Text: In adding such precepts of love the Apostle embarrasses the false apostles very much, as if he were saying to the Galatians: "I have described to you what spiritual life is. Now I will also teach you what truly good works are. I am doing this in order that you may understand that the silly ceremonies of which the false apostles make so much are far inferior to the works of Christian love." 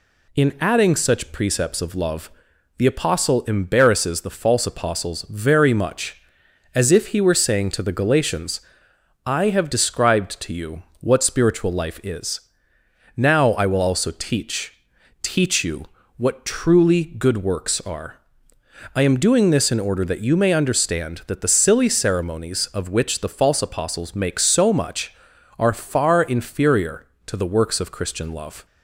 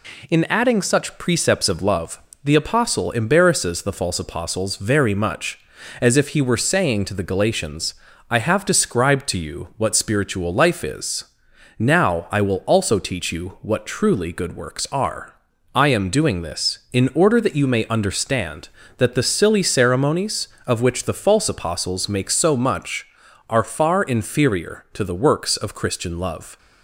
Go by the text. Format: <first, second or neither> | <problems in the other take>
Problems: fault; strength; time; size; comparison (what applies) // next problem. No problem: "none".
second | pauses between "love" and "the"; noticeable; at 2.3 s; 0.46 s long; slight in the second // pauses between "you" and "what"; slight; at 10.8 s; 0.18 s long // says "teach" twice; at 15.2 s // pauses between "you" and "what"; slight; at 15.8 s; 0.28 s long